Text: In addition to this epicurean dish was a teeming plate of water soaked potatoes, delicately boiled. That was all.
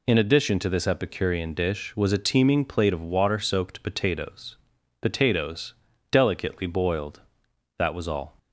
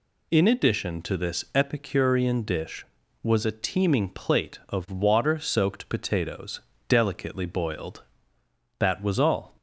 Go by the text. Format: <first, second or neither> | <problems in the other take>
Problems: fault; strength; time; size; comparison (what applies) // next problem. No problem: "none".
second | says "potatoes" twice; at 4.9 s